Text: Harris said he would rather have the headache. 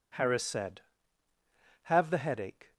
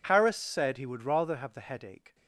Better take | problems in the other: second | skips "he would rather"; at 1.3 s

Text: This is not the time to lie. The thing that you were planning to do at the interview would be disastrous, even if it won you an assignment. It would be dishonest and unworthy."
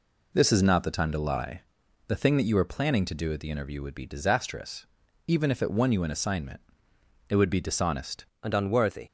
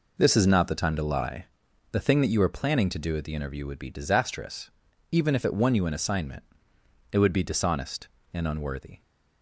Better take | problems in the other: second | changes voice at "and"; from 8.4 s on; 0.6 s long

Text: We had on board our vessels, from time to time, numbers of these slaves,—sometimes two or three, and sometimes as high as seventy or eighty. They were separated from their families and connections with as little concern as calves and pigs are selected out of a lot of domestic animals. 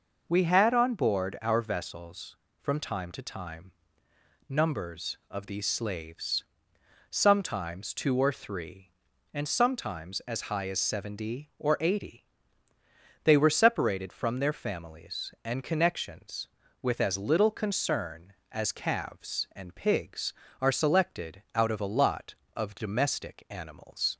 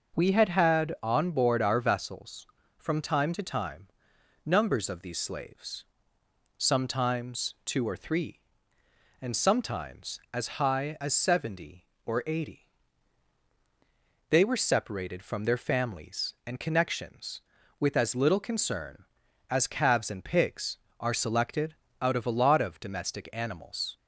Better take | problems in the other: first | says "had" twice; at 0.4 s // pauses between "selected" and "out"; slight; at 21.7 s; 0.28 s long

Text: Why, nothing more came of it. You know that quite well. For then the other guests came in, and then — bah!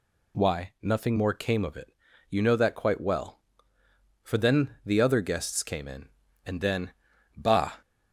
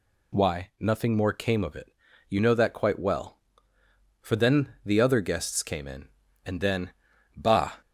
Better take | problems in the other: neither | none

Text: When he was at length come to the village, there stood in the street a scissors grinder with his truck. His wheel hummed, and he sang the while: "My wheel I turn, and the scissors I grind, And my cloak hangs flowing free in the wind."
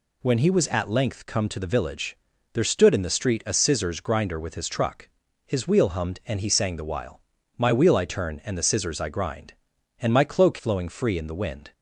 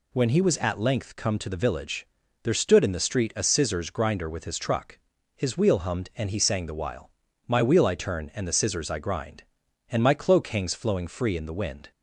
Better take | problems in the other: second | skips "hangs"; at 10.5 s

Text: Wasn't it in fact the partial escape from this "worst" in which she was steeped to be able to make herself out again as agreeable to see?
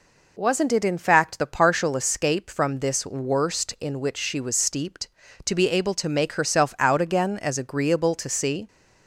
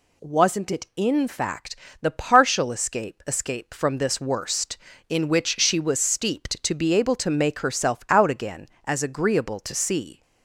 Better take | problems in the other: first | pauses between "fact" and "the"; slight; at 1.7 s; 0.26 s long // says "escape" twice; at 3.2 s

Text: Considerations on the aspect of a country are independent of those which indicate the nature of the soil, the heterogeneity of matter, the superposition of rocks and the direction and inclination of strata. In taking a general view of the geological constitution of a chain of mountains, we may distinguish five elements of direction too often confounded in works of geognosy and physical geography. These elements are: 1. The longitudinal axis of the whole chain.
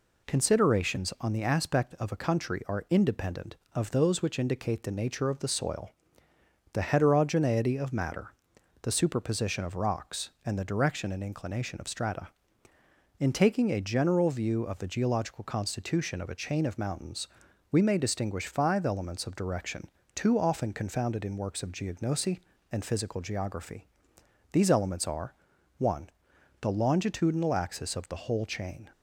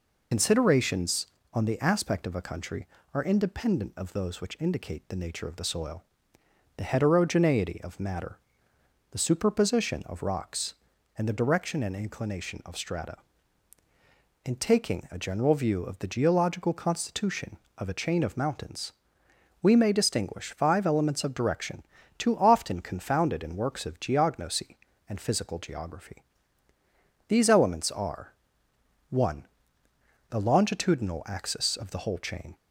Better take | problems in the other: first | loses the start of "Considerations"; at 0.3 s; 80 ms // pauses between "direction" and "too"; slight; at 21.8 s; 0.34 s long; slight in the first

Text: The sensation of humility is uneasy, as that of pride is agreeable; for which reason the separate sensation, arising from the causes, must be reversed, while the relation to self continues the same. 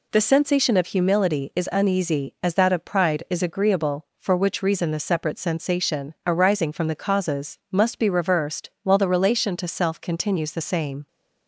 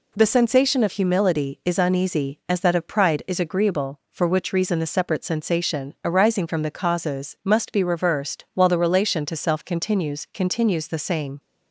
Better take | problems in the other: first | says "continues" twice; at 10.3 s

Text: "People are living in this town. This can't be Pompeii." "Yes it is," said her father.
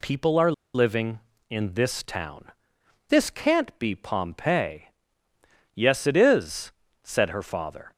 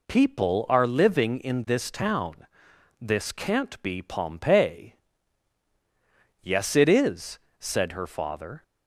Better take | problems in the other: second | pauses between "are" and "living"; slight; at 0.5 s; 0.22 s long

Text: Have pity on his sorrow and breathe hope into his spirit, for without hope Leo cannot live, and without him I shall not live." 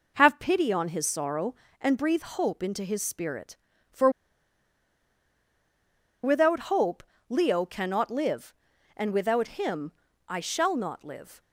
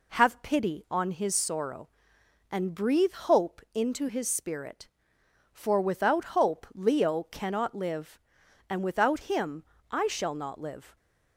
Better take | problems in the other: second | pauses between "for" and "without"; strong; at 4.0 s; 2.1 s long // pauses between "hope" and "Leo"; slight; at 7.0 s; 0.24 s long // pauses between "him" and "I"; slight; at 9.9 s; 0.34 s long; slight in the second

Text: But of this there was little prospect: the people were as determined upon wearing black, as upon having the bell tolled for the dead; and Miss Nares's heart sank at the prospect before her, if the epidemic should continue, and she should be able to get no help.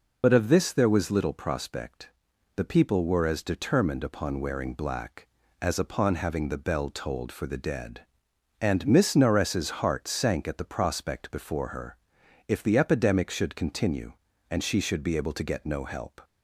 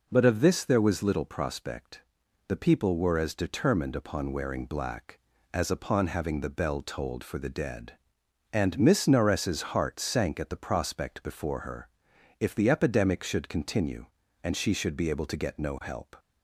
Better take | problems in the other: second | loses the start of "But"; at 0.2 s; 60 ms

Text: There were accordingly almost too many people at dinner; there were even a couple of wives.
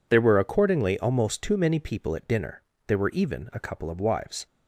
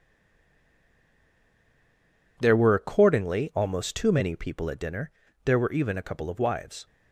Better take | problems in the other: first | stays silent before the first word; until 2.3 s; 2.3 s long

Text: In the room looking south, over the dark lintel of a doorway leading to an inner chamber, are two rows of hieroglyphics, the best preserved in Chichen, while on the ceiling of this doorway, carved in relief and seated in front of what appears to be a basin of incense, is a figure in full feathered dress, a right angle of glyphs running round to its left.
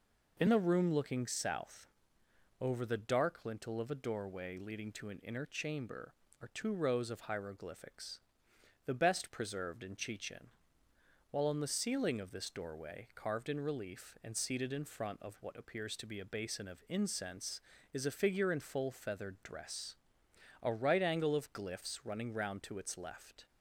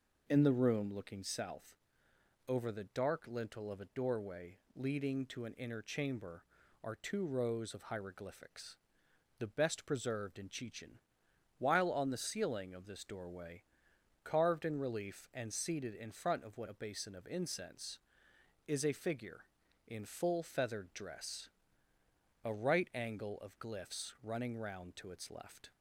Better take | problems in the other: first | pauses between "doorway" and "leading"; slight; at 4.5 s; 0.18 s long // skips "appears to be"; at 16.6 s

